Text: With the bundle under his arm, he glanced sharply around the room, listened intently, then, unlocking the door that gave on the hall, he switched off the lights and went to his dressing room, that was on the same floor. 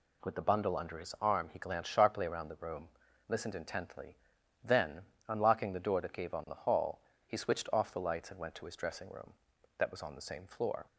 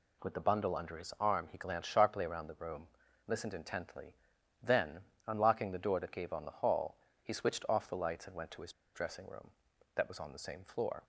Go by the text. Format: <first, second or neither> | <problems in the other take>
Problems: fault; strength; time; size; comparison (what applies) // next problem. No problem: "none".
first | pauses between "his" and "dressing"; slight; at 8.7 s; 0.21 s long